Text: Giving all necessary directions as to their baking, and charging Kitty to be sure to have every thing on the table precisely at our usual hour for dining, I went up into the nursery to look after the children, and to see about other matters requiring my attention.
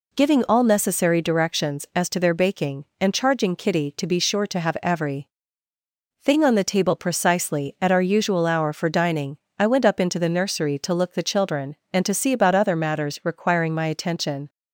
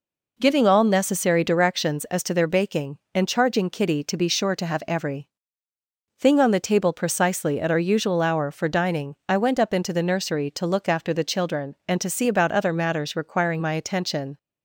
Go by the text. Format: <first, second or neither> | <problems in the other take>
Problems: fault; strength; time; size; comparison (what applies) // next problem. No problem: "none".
second | pauses between "every" and "thing"; noticeable; at 5.2 s; 0.92 s long; noticeable in the second // skips "after"; at 11.1 s